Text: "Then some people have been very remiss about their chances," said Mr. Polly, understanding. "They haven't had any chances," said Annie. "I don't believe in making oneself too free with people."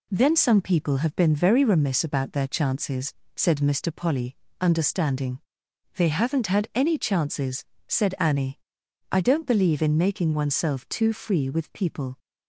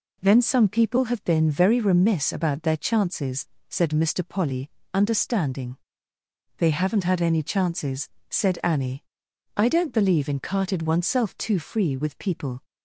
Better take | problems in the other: first | says "carted" for "making"; at 10.4 s

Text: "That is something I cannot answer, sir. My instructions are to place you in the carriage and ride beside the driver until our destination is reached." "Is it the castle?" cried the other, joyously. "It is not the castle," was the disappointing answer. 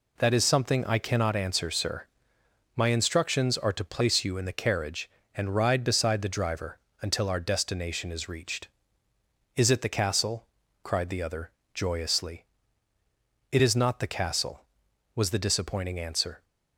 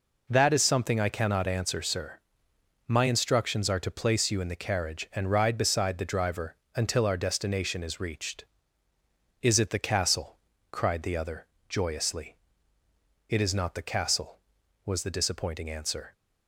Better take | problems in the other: neither | pauses between "driver" and "until"; slight; the same in both

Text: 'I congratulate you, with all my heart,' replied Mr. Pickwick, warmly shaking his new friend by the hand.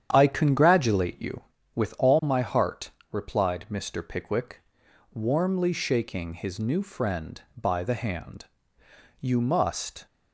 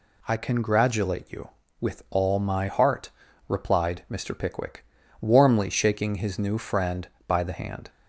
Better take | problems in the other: second | starts louder than the rest; strong; until 1.1 s; 9 dB // goes on to say "You must"; noticeable; from 9.1 s on; 0.86 s long

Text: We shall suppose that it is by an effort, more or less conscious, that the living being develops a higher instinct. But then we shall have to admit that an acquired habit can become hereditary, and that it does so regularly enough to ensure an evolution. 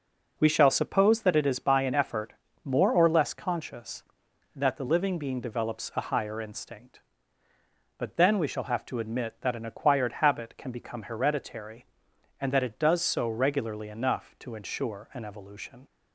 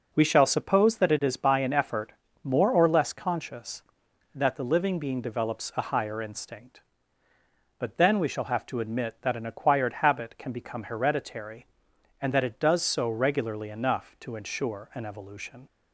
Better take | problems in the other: neither | none

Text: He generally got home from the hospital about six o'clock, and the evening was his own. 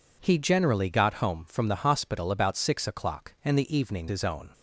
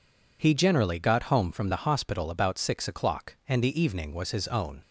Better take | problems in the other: second | skips "was"; at 4.0 s

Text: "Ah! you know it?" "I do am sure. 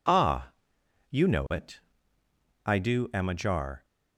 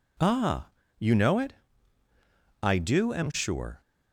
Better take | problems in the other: second | says "ajar" for "sure"; at 3.2 s

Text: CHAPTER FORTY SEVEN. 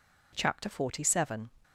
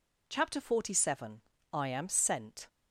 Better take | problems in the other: first | goes on to say "I AM SENT"; noticeable; from 1.7 s on; 0.94 s long

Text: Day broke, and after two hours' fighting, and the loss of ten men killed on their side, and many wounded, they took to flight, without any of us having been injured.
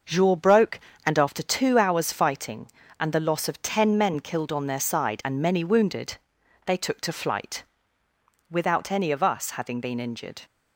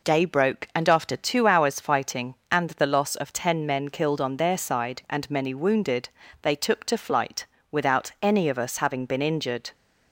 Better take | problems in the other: second | starts louder than the rest; noticeable; until 1.3 s; 6 dB // says "Jour" for "Day"; at 0.0 s

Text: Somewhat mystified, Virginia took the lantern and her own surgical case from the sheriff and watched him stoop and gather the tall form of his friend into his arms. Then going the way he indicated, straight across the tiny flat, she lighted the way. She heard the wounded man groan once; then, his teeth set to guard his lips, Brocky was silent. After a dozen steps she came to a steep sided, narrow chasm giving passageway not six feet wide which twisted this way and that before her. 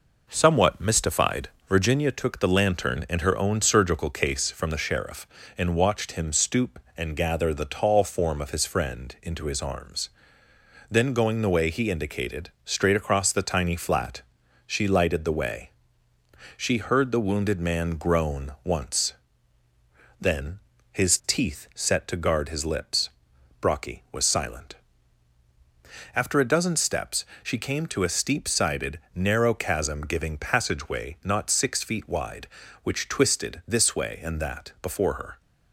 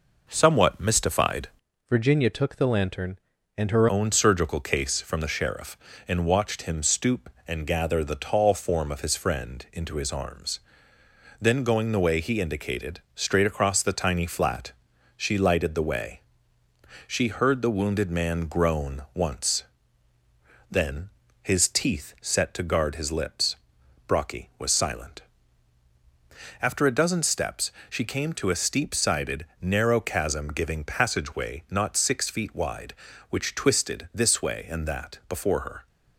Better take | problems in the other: first | changes voice from "Virginia" to "her"; from 1.8 to 3.8 s; 2.0 s long // pauses between "steps" and "she"; slight; at 27.7 s; 0.18 s long; slight in the first

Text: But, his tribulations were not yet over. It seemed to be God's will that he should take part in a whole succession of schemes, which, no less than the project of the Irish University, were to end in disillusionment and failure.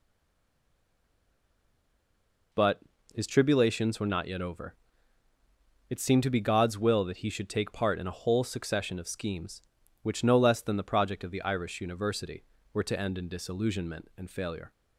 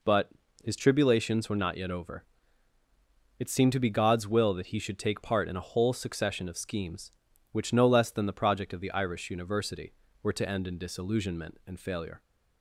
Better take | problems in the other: second | stays silent before the first word; strong; until 2.5 s; 2.5 s long

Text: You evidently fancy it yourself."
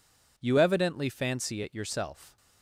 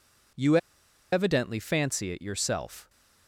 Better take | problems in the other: first | pauses between "You" and "evidently"; noticeable; at 0.5 s; 0.55 s long

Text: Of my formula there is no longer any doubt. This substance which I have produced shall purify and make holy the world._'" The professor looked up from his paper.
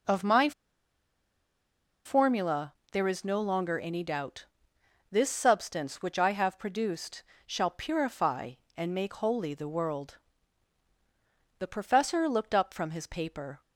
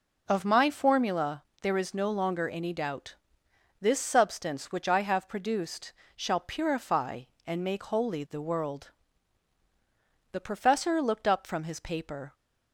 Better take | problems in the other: second | pauses between "my" and "formula"; strong; at 0.5 s; 1.5 s long // pauses between "formula" and "there"; slight; at 2.7 s; 0.18 s long; slight in the second // pauses between "produced" and "shall"; slight; at 7.2 s; 0.24 s long; slight in the second

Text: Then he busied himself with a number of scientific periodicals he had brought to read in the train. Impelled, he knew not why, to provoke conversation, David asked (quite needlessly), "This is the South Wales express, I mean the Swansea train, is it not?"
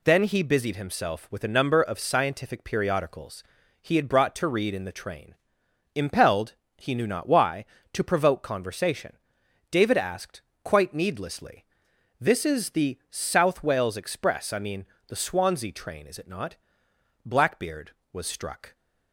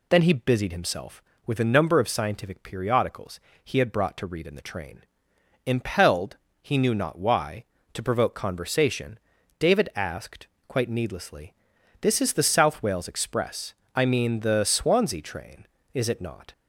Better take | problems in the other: second | pauses between "periodicals" and "he"; at 3.4 s; 0.38 s long; slight in the second // pauses between "mean" and "the"; slight; at 14.8 s; 0.22 s long // goes on to say "Blackbeard was struck"; from 17.2 s on; 1.5 s long

